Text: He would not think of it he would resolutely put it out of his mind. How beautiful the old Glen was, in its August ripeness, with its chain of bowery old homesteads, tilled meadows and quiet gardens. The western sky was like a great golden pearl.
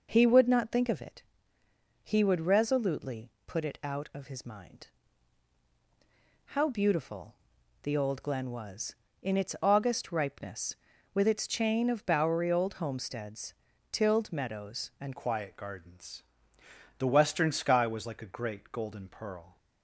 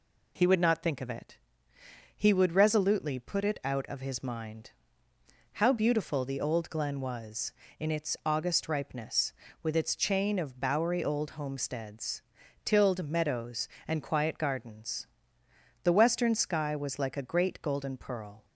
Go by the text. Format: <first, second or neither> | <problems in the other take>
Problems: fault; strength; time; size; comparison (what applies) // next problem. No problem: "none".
second | pauses between "it" and "he"; noticeable; at 1.2 s; 0.80 s long; noticeable in the second // pauses between "resolutely" and "put"; slight; at 3.2 s; 0.16 s long // pauses between "beautiful" and "the"; noticeable; at 7.3 s; 0.48 s long // changes voice at "quiet"; from 15.1 s on; 4.4 s long